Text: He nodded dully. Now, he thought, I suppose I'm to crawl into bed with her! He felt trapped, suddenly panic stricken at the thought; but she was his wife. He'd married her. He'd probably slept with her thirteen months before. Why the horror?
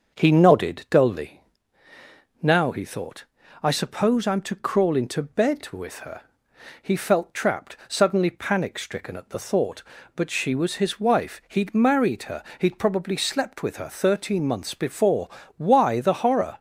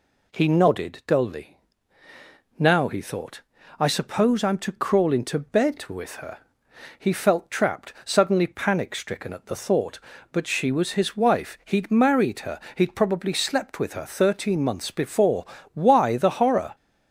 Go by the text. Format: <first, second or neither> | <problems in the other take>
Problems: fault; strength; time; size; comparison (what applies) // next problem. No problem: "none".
second | starts louder than the rest; until 1.6 s; 6.5 dB